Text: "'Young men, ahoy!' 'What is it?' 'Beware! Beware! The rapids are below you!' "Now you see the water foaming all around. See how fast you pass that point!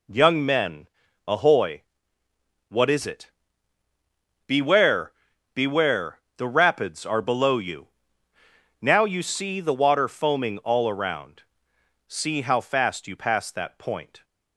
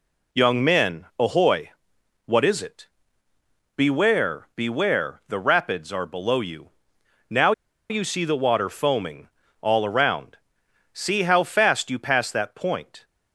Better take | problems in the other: first | pauses between "Now" and "you"; at 7.5 s; 0.38 s long // pauses between "foaming" and "all"; slight; at 9.2 s; 0.32 s long

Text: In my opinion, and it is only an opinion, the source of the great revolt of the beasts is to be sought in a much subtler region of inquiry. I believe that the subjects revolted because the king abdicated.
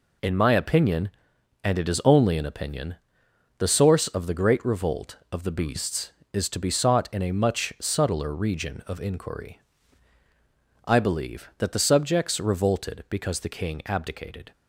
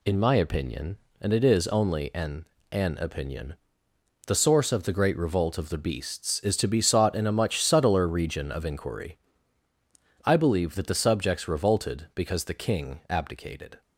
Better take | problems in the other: first | says "an" twice; at 2.7 s

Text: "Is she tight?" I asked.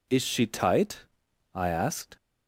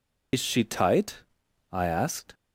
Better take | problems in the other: first | loses the start of "Is"; at 0.3 s; 55 ms

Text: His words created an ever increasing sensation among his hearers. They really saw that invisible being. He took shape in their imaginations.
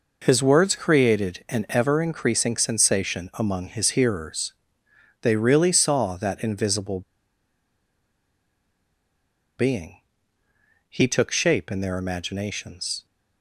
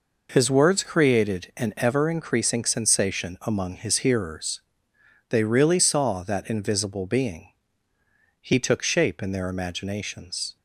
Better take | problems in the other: second | pauses between "invisible" and "being"; strong; at 7.0 s; 2.5 s long

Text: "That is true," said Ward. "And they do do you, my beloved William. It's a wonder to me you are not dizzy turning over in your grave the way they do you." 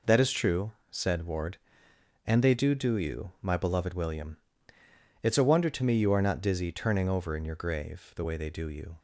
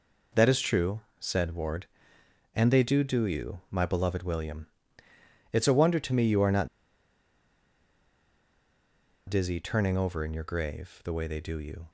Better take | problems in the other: first | pauses between "not" and "dizzy"; strong; at 6.6 s; 2.6 s long

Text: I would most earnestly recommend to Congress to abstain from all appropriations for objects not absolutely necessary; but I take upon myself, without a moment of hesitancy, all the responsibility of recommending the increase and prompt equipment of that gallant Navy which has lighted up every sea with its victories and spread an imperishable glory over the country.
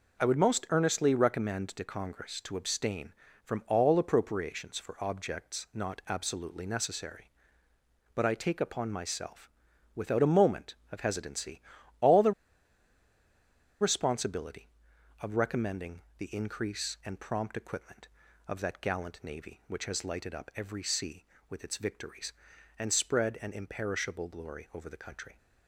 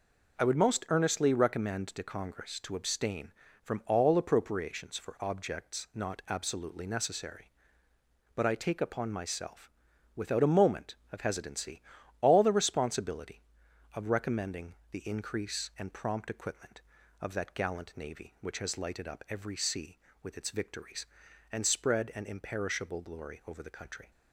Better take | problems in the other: second | pauses between "the" and "responsibility"; strong; at 12.3 s; 1.4 s long // pauses between "recommending" and "the"; slight; at 16.0 s; 0.18 s long; slight in the second

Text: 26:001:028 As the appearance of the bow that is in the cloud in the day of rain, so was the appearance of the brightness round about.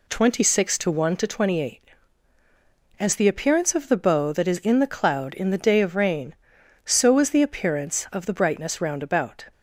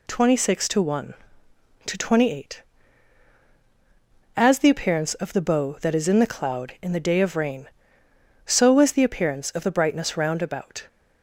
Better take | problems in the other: neither | none

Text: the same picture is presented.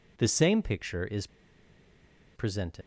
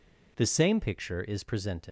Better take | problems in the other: second | pauses between "is" and "presented"; at 1.2 s; 1.0 s long

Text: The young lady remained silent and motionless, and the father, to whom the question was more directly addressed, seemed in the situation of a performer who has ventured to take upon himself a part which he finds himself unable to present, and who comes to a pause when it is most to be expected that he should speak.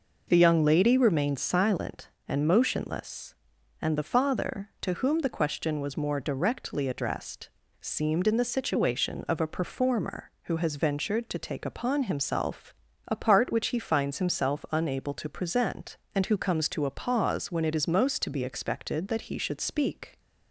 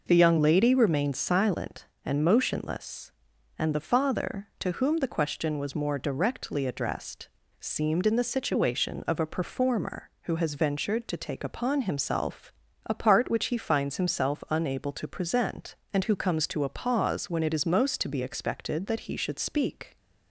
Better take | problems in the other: neither | pauses between "himself" and "a"; slight; the same in both

